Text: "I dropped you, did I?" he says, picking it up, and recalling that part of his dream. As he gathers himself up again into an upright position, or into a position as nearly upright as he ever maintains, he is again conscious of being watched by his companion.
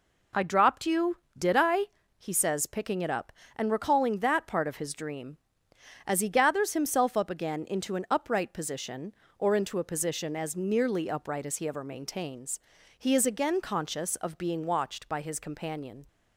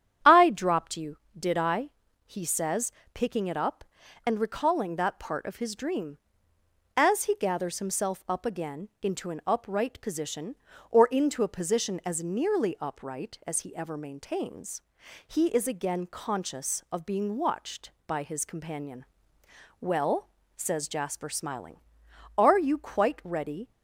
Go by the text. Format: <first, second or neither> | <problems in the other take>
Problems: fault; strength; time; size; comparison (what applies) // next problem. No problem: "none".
first | starts louder than the rest; strong; until 1.4 s; 9.5 dB // goes on to say "Well says Jasper smiling are you quite ready"; strong; from 19.7 s on; 3.9 s long